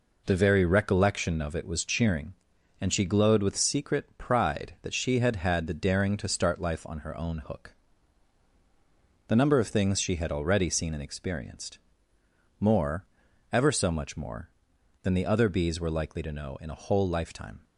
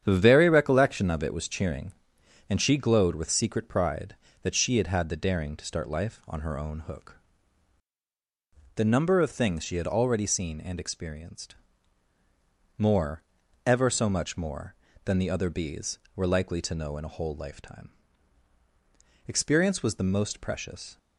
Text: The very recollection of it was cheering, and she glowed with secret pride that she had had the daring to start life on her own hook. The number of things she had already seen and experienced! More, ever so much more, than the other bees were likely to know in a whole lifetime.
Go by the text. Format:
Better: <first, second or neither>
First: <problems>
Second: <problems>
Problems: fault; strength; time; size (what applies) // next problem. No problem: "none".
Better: first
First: none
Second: starts louder than the rest; strong; until 1.0 s; 9 dB // goes on to say "Experience was the most precious"; strong; from 19.2 s on; 1.7 s long